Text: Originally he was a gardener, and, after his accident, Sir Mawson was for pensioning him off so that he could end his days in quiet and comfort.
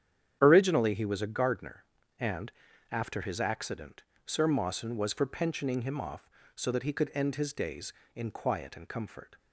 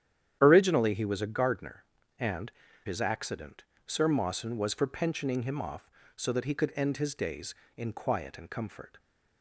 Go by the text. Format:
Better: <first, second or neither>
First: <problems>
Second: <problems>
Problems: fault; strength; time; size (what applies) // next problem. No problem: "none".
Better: first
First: starts louder than the rest; strong; until 1.4 s; 9 dB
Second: starts louder than the rest; strong; until 1.4 s; 10 dB // skips "after"; at 2.6 s